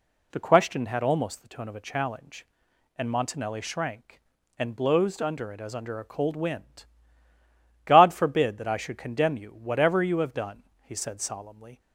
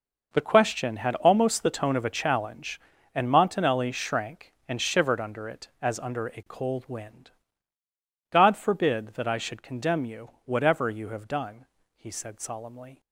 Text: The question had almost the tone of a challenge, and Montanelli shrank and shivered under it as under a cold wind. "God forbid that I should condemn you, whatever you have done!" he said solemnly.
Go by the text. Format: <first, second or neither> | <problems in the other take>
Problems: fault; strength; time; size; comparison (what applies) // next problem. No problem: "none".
second | says "blowsed" for "shivered"; at 4.7 s